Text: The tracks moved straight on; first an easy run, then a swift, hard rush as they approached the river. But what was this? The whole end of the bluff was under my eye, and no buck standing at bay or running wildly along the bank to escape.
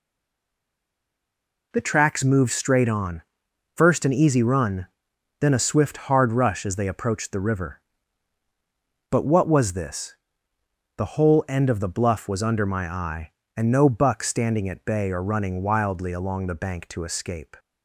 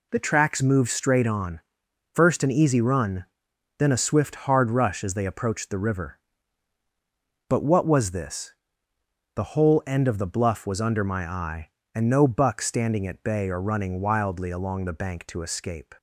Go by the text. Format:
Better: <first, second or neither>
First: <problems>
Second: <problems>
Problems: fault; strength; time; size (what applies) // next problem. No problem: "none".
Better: second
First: stays silent before the first word; noticeable; until 1.7 s; 1.7 s long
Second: none